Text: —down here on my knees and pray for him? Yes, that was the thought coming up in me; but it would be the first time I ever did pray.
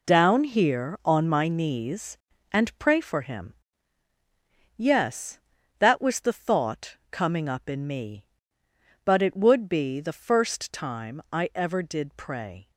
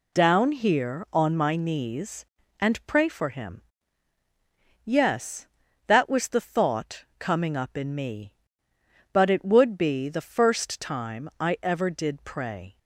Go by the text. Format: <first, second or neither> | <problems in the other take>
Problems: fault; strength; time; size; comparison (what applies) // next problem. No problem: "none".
second | gets quieter; strong; throughout; 10.5 dB